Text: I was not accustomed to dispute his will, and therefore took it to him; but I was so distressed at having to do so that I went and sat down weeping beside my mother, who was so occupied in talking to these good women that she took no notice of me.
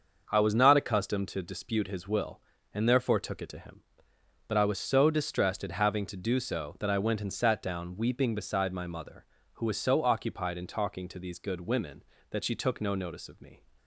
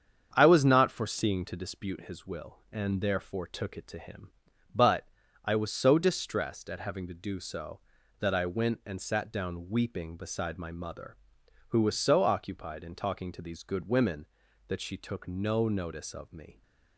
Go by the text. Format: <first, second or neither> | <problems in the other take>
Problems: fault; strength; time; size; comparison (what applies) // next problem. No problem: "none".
first | starts louder than the rest; strong; until 1.3 s; 7.5 dB; also in the first // says "foreseeing" for "accustomed"; at 0.8 s // pauses between "but" and "I"; at 5.0 s; 0.38 s long